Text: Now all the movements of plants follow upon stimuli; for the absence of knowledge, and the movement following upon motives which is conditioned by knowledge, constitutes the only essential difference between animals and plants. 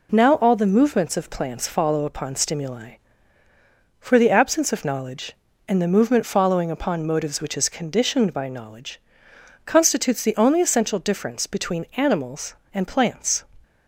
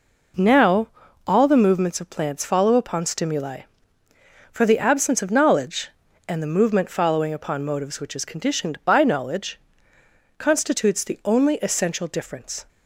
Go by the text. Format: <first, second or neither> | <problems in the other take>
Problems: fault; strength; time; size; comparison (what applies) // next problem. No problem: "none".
first | pauses between "Now" and "all"; at 0.8 s; 0.38 s long // stops before "between animals and plants"; at 12.6 s